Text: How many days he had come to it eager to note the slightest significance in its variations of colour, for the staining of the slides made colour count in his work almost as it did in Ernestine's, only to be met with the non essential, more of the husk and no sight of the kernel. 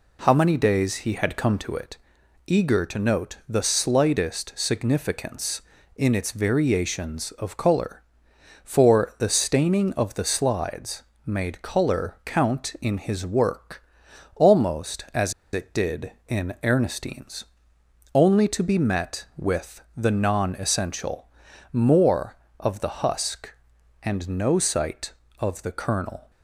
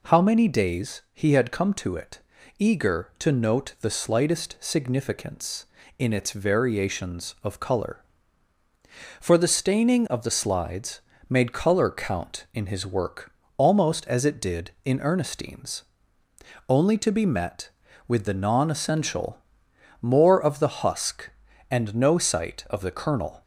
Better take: second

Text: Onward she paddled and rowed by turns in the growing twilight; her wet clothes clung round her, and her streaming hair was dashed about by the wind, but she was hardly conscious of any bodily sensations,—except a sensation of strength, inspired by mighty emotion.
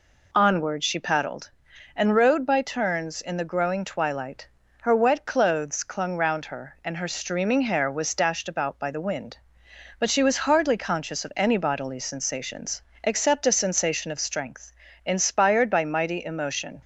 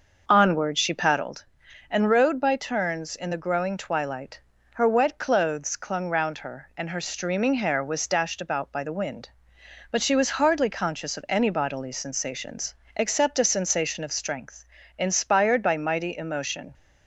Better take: first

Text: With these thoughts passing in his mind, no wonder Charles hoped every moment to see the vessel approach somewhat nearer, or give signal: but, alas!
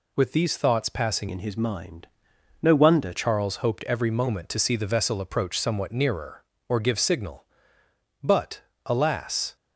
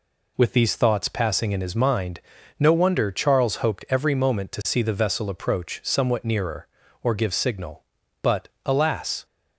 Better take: second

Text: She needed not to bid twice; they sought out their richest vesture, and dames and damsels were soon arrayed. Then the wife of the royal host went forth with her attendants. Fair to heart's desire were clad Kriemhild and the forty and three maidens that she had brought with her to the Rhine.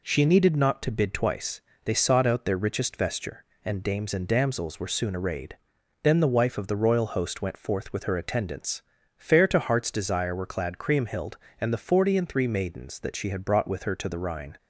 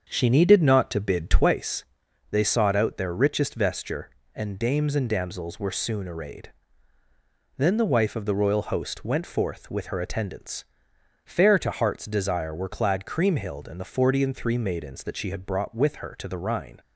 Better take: first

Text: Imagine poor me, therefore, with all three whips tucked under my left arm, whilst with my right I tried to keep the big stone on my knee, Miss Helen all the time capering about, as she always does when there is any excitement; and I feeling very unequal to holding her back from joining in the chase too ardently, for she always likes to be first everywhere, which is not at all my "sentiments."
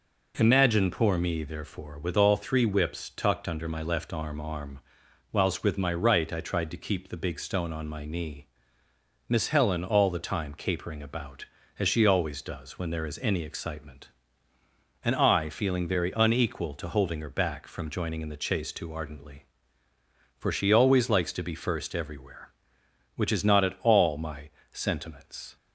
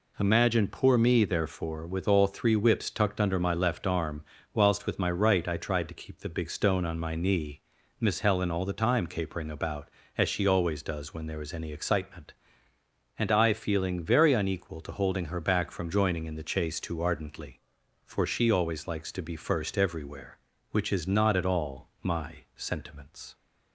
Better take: second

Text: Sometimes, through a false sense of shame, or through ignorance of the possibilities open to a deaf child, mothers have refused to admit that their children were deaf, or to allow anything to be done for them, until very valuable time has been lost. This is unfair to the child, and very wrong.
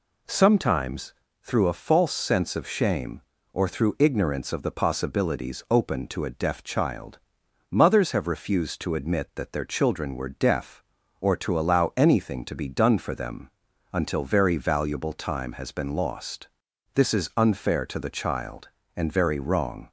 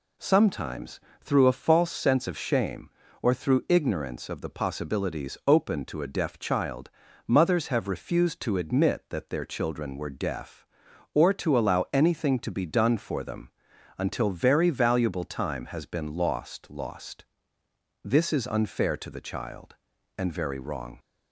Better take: first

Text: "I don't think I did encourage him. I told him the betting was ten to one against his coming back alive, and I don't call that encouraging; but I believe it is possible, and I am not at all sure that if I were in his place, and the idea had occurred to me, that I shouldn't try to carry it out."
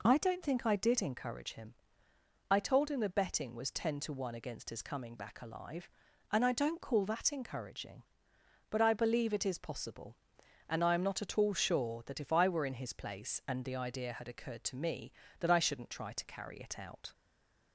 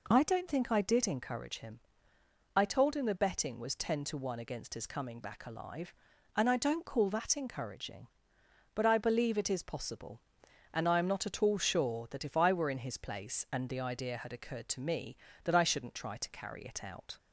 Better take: second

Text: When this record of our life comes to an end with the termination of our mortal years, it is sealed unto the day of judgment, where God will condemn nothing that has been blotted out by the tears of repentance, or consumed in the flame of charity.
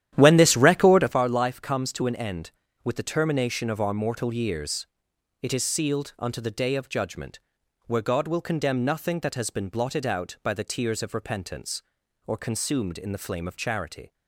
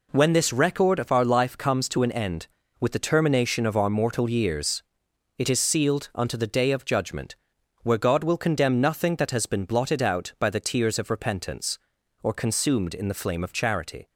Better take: second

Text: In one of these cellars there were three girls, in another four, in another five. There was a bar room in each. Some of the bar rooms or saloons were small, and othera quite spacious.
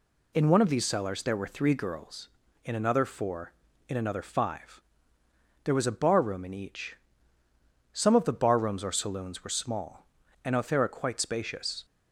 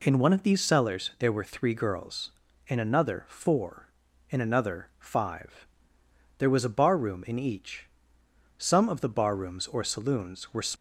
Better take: first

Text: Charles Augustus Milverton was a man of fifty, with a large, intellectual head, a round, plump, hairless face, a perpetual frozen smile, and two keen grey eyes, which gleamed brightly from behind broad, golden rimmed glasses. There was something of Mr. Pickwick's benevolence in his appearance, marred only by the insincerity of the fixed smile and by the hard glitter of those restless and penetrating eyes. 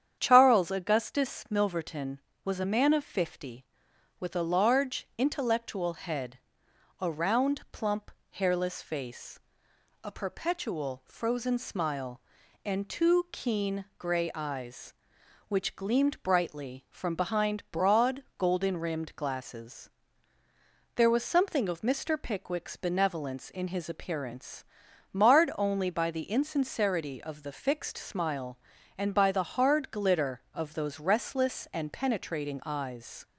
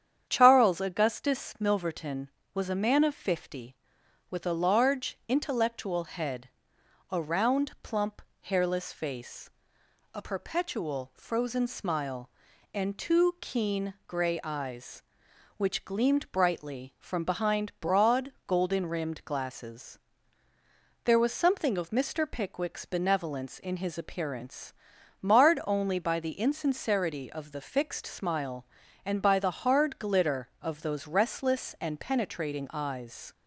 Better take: neither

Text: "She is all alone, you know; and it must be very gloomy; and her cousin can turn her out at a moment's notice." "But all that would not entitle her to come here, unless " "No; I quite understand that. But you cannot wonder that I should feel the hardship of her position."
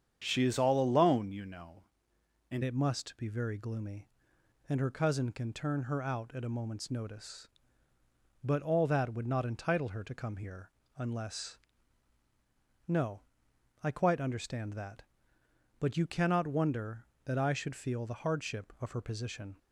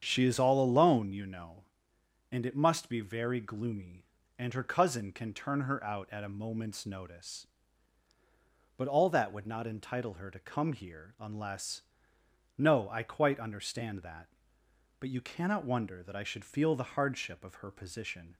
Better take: second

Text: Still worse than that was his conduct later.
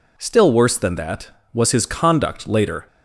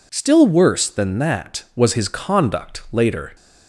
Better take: neither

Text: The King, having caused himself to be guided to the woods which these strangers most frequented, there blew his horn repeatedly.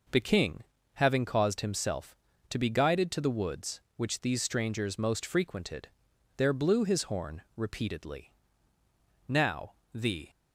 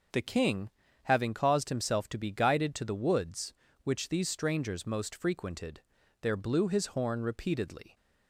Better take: second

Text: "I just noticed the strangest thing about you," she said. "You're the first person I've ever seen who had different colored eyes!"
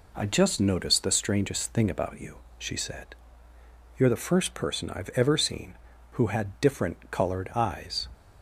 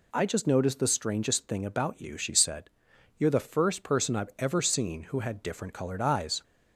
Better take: neither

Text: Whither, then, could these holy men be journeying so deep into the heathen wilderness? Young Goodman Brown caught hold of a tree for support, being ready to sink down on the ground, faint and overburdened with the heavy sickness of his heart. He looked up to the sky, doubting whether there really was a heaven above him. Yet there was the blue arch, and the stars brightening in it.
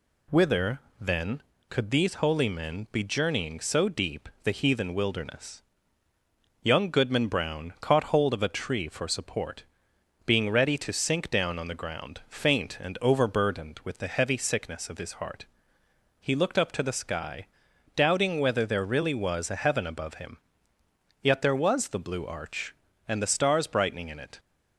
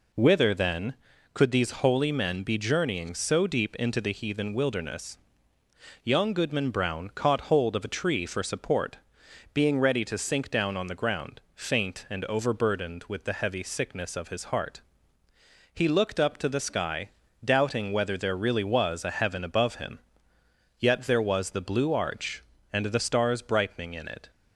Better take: second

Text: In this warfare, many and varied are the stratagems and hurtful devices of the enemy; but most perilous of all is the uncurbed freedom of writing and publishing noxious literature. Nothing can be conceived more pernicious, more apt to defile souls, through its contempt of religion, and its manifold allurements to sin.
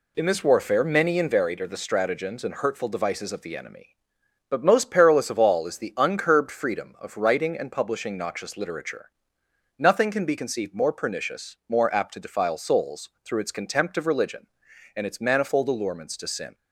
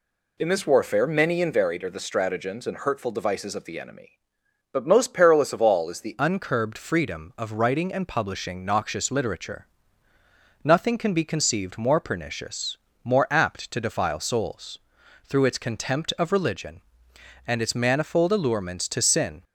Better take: first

